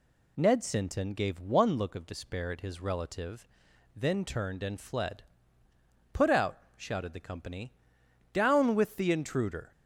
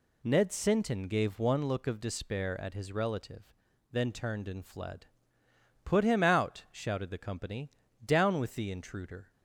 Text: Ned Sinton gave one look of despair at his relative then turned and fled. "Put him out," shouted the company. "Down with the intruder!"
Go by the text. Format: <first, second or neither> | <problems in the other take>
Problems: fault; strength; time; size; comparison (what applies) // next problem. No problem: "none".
second | pauses between "relative" and "then"; noticeable; at 3.4 s; 0.46 s long; also in the second // skips "him"; at 6.2 s